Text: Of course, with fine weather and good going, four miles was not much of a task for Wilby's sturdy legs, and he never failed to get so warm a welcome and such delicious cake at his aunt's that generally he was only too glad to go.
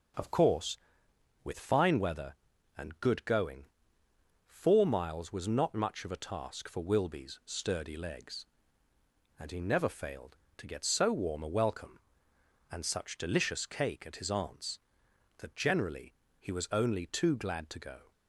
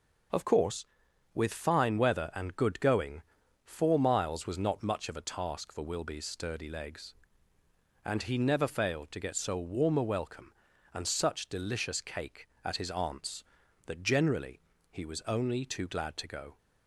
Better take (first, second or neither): neither